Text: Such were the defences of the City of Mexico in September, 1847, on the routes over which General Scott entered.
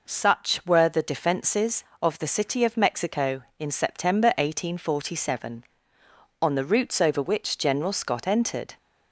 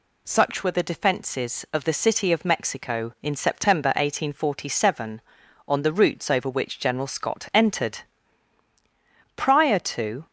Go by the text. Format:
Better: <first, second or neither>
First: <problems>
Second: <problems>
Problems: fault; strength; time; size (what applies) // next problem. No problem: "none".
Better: first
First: none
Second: goes on to say "Prior to"; noticeable; from 9.3 s on; 0.90 s long